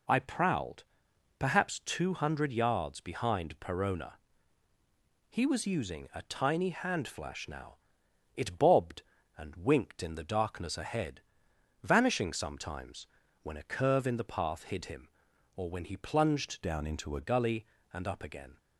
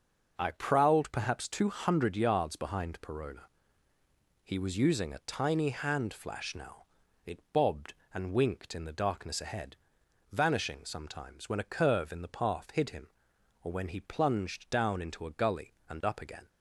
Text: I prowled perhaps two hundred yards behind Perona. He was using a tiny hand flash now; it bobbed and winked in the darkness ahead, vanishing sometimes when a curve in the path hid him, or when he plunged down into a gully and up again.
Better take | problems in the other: second | pauses between "prowled" and "perhaps"; noticeable; at 0.8 s; 0.56 s long // pauses between "sometimes" and "when"; slight; at 13.0 s; 0.34 s long // changes voice from "down" to "a"; from 16.6 to 17.1 s; 0.5 s long

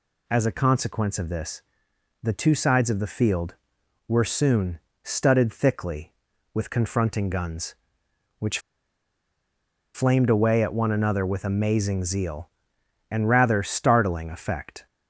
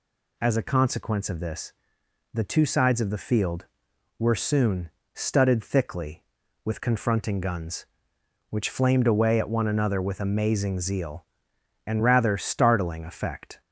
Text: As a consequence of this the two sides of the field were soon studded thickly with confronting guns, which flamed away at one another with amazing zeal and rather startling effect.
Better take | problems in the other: second | pauses between "this" and "the"; noticeable; at 1.6 s; 0.58 s long; noticeable in the second // pauses between "soon" and "studded"; slight; at 4.8 s; 0.24 s long; slight in the second // pauses between "which" and "flamed"; strong; at 8.5 s; 1.3 s long

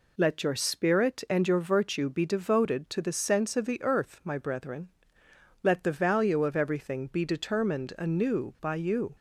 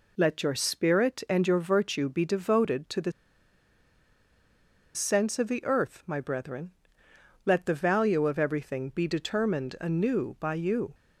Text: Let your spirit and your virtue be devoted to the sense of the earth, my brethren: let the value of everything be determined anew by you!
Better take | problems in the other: first | pauses between "the" and "sense"; strong; at 3.1 s; 1.8 s long

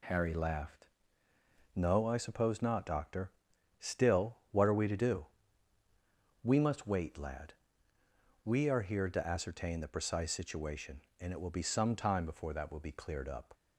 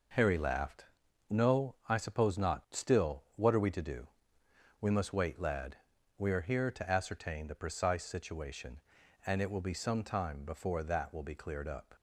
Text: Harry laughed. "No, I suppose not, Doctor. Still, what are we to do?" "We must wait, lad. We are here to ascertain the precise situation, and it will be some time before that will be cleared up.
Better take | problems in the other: first | skips "Doctor"; at 2.6 s

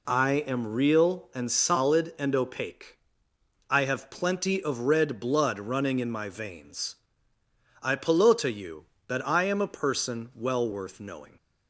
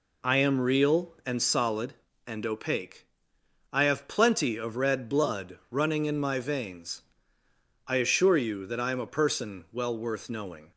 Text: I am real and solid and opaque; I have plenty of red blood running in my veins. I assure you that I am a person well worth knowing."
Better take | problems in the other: second | says "pelota" for "assure"; at 7.9 s

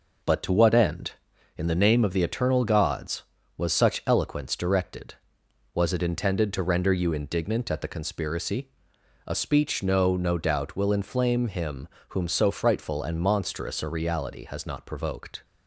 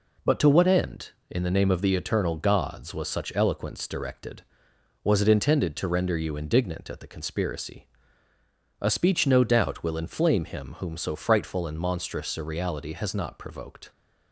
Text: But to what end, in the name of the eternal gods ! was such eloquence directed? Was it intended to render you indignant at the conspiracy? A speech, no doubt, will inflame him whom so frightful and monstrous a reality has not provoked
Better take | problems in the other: second | says "no" twice; at 10.1 s // pauses between "him" and "whom"; slight; at 11.8 s; 0.22 s long

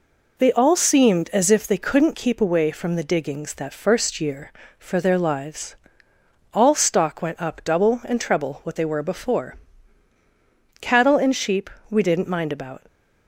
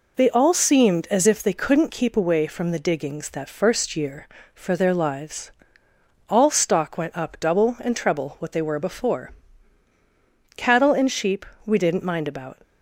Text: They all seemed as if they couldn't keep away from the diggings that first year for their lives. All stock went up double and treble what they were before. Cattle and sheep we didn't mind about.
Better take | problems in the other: neither | pauses between "sheep" and "we"; slight; the same in both

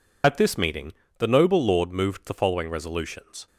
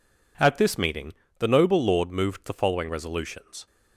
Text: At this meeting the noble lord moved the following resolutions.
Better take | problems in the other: second | loses the start of "At"; at 0.2 s; 95 ms // pauses between "meeting" and "the"; slight; at 0.9 s; 0.24 s long; slight in the second

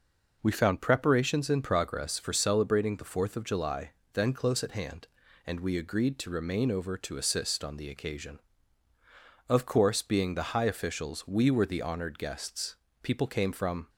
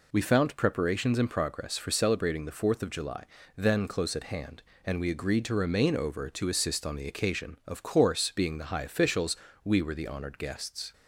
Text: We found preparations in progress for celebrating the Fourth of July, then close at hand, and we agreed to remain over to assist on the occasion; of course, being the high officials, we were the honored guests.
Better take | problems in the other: second | goes on to say "People came from"; noticeable; from 13.0 s on; 0.86 s long

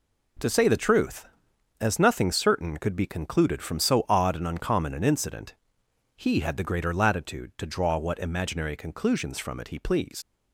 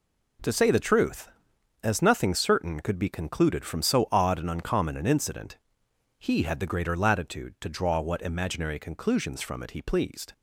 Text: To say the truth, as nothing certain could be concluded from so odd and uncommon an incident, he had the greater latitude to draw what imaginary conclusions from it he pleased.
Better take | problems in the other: second | leaves "pleased" unfinished; at 10.2 s; 75 ms

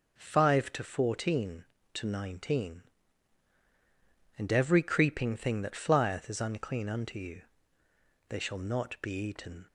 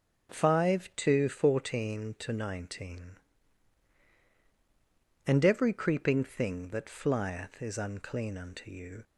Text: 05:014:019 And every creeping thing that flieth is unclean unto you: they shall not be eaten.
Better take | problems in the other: first | starts louder than the rest; strong; until 1.3 s; 7 dB // stops before "they shall not be eaten"; at 9.0 s

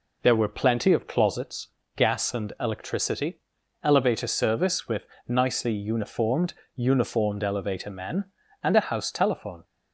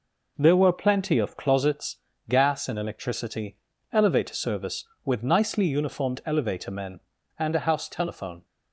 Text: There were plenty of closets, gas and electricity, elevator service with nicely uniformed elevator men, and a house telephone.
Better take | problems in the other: second | pauses between "with" and "nicely"; slight; at 5.0 s; 0.22 s long // says "uniformed" twice; at 6.7 s

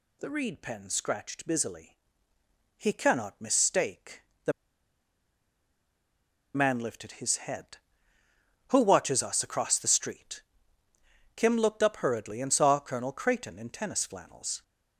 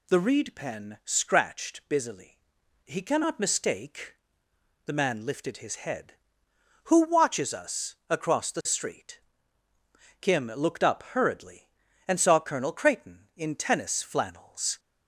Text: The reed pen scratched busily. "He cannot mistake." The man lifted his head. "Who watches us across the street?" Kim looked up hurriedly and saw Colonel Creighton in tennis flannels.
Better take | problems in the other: second | pauses between "The" and "man"; strong; at 4.5 s; 2.0 s long

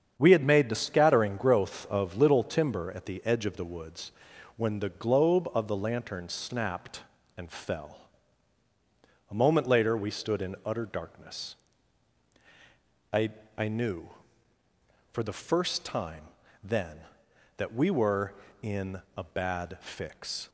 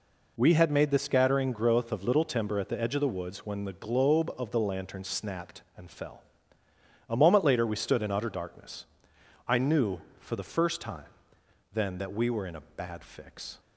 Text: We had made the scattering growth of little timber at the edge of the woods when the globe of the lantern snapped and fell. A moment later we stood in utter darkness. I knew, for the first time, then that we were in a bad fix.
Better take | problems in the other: second | starts louder than the rest; strong; until 1.1 s; 7.5 dB // pauses between "woods" and "when"; noticeable; at 4.1 s; 0.46 s long // says "I" twice; at 13.5 s

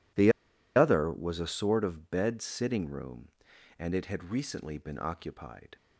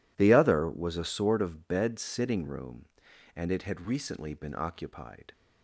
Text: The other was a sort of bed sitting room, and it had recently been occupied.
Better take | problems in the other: second | pauses between "The" and "other"; at 0.3 s; 0.44 s long

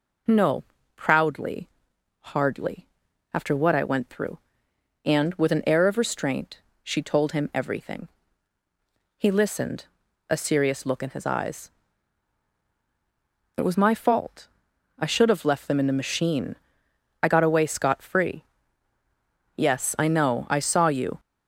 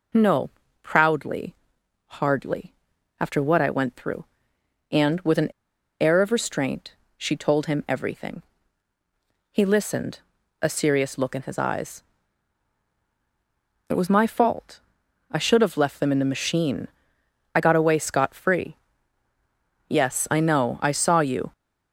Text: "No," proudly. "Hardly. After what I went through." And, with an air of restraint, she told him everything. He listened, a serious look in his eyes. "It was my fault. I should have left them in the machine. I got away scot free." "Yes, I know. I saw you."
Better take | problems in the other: first | pauses between "an" and "air"; noticeable; at 5.5 s; 0.50 s long

